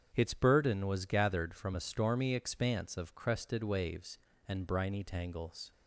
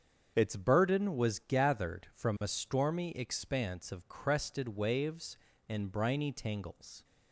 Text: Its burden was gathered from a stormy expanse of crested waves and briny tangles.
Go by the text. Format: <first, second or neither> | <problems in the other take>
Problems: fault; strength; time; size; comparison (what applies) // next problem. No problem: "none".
neither | starts louder than the rest; strong; the same in both